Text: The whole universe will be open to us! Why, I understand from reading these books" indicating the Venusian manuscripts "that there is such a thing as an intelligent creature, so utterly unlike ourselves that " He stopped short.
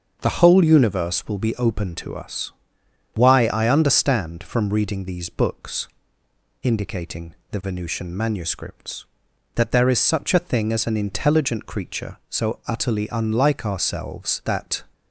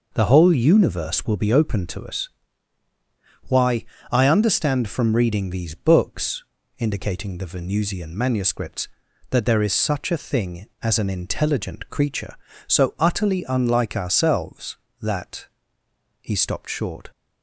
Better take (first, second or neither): second